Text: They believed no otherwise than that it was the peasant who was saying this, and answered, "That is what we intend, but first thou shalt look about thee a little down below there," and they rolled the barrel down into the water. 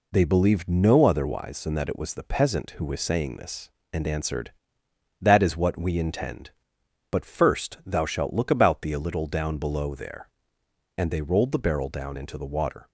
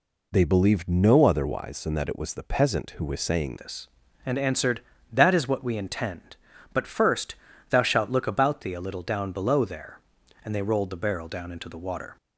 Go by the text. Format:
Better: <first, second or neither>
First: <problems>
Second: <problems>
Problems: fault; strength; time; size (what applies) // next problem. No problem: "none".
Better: first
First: none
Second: changes voice at "this"; from 3.5 s on; 8.6 s long // pauses between "first" and "thou"; slight; at 7.3 s; 0.36 s long